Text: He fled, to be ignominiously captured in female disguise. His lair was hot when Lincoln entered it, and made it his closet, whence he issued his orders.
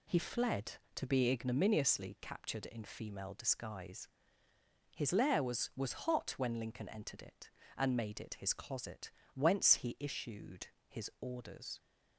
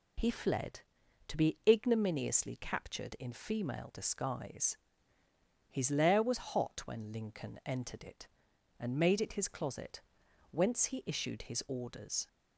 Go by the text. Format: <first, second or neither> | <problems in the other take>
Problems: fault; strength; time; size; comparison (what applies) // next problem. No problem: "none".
second | says "was" twice; at 5.7 s // pauses between "issued" and "his"; slight; at 10.6 s; 0.22 s long